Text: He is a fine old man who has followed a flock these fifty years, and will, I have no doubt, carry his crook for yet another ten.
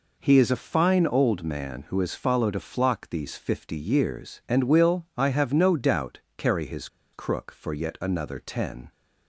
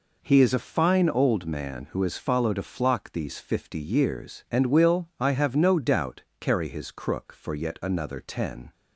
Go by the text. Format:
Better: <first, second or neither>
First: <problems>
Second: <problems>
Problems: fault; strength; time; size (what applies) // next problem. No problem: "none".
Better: second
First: pauses between "his" and "crook"; slight; at 6.8 s; 0.25 s long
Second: none